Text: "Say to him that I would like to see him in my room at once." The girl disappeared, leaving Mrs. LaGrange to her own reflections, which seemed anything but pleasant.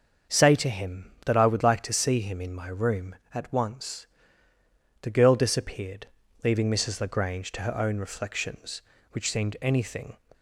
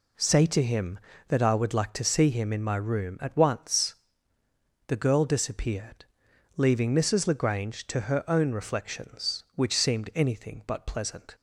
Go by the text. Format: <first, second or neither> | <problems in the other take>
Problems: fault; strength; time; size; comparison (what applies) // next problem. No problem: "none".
second | starts louder than the rest; until 1.4 s; 6.5 dB // stops before "but pleasant"; at 10.3 s